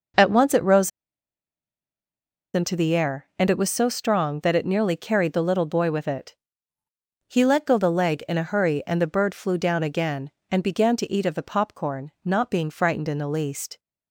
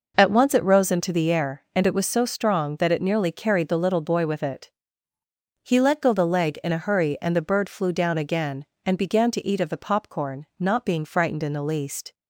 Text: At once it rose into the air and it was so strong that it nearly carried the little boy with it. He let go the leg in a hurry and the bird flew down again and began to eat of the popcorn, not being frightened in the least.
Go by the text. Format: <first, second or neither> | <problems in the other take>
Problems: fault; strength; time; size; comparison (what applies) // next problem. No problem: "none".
second | pauses between "rose" and "into"; strong; at 0.9 s; 1.6 s long